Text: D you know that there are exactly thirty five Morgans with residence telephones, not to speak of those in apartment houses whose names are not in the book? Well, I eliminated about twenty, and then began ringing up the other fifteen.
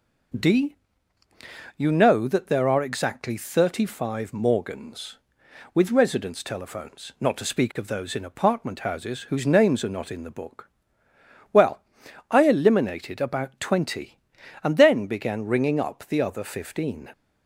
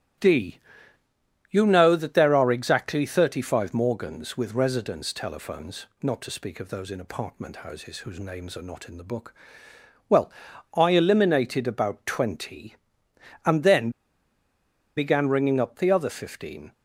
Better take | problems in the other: first | starts louder than the rest; strong; until 2.1 s; 13 dB // pauses between "D" and "you"; noticeable; at 0.5 s; 0.92 s long; also in the first // pauses between "then" and "began"; at 13.8 s; 1.0 s long

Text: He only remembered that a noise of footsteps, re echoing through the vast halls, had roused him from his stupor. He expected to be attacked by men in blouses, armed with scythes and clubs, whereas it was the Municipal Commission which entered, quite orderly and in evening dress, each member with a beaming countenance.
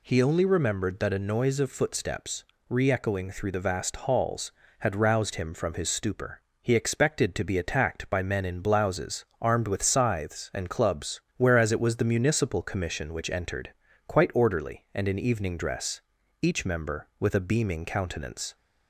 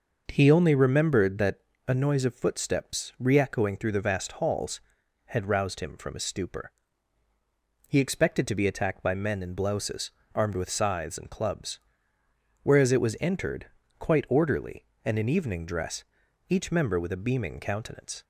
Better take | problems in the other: first | pauses between "that" and "a"; slight; at 1.5 s; 0.26 s long // skips "the Municipal Commission which"; at 13.1 s

